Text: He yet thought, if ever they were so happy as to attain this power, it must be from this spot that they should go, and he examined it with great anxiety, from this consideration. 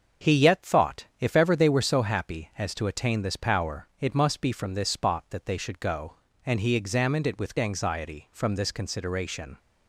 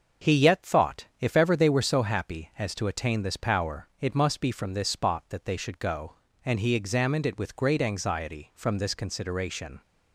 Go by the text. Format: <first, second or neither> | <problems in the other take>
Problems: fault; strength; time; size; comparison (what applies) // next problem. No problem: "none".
second | starts louder than the rest; until 1.3 s; 6.5 dB; noticeable in the second // skips "great"; at 7.5 s